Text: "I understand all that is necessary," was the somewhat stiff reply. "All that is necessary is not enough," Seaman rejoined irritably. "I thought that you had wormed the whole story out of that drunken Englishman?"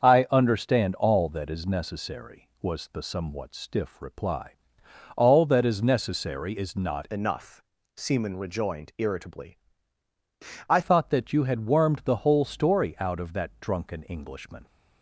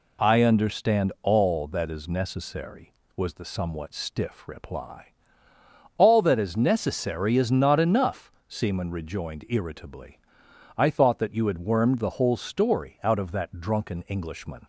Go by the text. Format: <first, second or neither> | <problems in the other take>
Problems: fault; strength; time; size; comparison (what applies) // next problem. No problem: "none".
second | starts louder than the rest; until 1.0 s; 7 dB // changes voice from "enough" to "I"; from 7.1 to 10.8 s; 3.7 s long